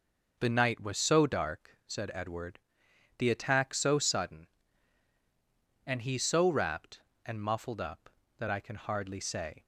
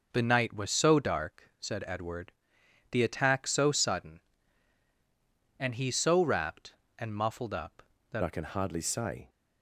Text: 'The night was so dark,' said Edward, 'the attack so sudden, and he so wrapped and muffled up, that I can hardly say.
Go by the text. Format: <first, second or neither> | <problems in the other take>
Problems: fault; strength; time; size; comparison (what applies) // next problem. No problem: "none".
first | changes voice at "I"; from 8.2 s on; 1.0 s long